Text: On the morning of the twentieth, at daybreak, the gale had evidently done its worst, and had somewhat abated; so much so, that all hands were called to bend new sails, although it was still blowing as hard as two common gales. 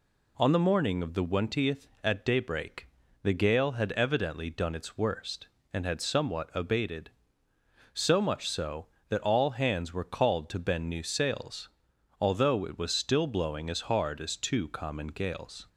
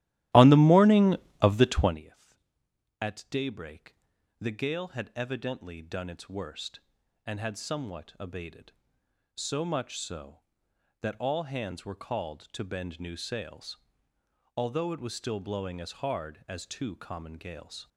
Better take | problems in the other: first | starts louder than the rest; strong; until 2.0 s; 15 dB

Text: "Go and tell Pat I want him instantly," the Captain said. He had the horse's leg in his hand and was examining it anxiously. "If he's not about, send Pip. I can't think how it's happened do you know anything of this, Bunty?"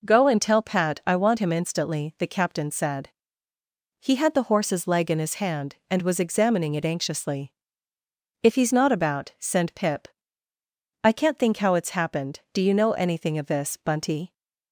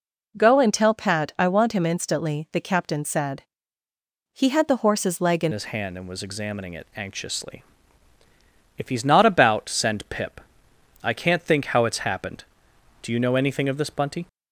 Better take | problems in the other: first | changes voice at "his"; from 5.5 s on; 8.7 s long

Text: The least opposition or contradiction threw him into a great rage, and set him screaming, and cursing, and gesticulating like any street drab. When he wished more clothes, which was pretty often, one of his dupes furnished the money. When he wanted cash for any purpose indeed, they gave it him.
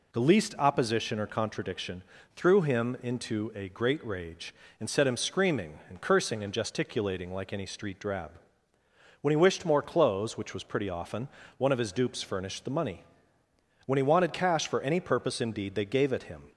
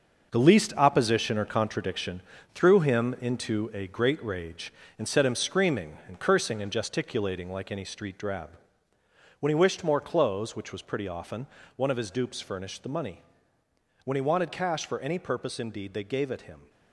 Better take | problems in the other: first | gets quieter; strong; throughout; 9 dB // pauses between "contradiction" and "threw"; slight; at 2.2 s; 0.32 s long; slight in the first

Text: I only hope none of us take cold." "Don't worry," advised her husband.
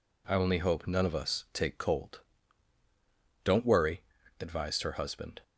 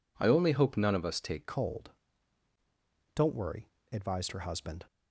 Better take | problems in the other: first | changes voice at "cold"; from 1.4 s on; 3.4 s long

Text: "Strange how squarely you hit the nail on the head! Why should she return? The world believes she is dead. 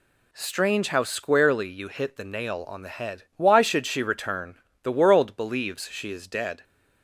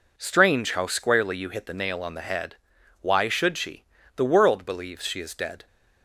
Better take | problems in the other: first | skips "return"; at 3.9 s

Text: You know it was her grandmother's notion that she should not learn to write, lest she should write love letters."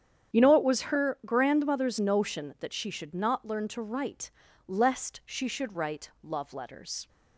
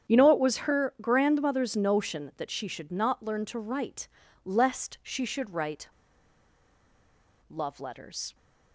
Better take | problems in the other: first | starts louder than the rest; strong; until 1.1 s; 8.5 dB; strong in the first // pauses between "write" and "love"; strong; at 5.8 s; 1.6 s long

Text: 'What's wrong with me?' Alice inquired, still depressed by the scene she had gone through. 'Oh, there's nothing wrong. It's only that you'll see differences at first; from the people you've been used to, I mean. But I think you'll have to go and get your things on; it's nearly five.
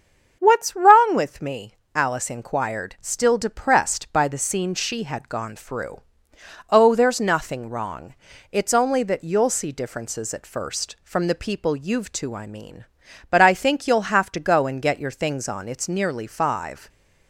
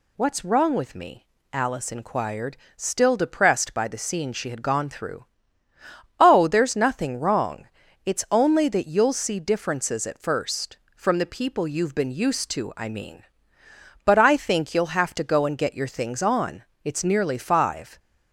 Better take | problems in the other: second | starts louder than the rest; strong; until 1.4 s; 7 dB // skips "been used"; at 12.1 s

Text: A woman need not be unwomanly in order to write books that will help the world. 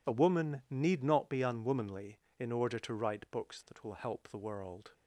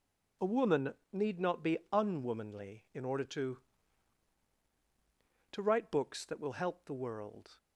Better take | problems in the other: first | pauses between "woman" and "need"; slight; at 0.9 s; 0.20 s long // says "to" twice; at 5.5 s

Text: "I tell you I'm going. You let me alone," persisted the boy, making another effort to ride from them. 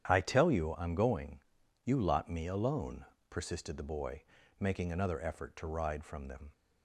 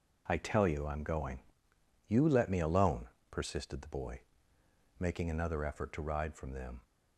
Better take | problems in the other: second | starts louder than the rest; strong; until 1.1 s; 9.5 dB // says "lot" for "let"; at 2.0 s

